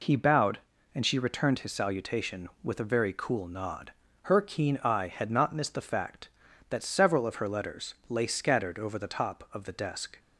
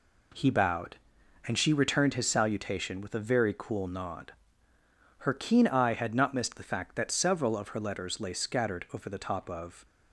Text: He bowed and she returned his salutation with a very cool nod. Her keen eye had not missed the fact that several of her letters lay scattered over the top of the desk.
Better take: first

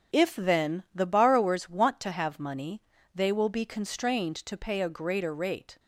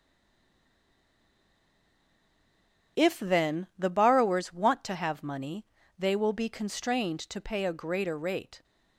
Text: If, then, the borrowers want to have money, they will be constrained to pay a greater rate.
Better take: first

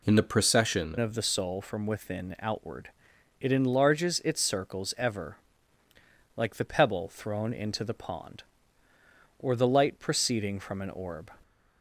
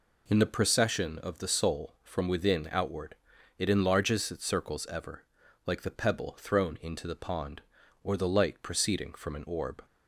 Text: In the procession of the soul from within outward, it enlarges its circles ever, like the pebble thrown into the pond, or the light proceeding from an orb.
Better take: second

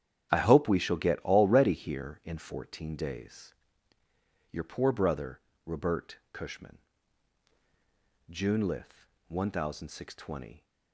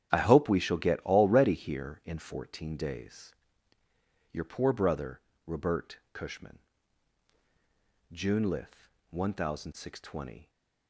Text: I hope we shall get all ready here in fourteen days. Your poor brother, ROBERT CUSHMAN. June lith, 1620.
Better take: neither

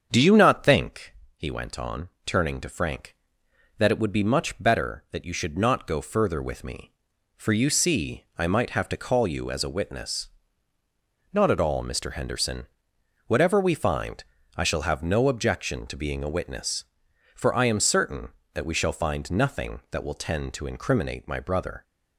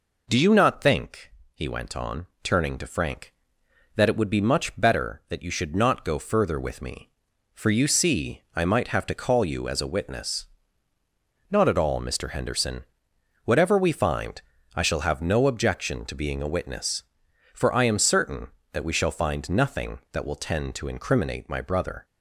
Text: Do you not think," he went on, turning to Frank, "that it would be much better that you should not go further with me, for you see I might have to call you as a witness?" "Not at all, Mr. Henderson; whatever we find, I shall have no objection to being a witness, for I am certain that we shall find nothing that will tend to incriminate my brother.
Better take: second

